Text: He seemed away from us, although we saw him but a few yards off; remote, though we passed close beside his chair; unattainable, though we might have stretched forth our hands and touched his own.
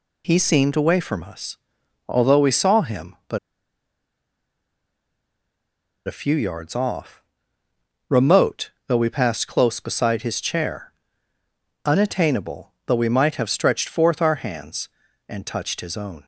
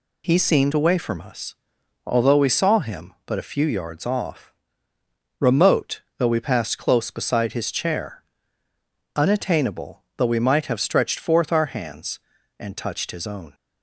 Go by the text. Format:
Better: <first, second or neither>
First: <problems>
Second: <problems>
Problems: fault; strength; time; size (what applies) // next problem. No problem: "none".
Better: second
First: pauses between "but" and "a"; strong; at 3.3 s; 2.6 s long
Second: none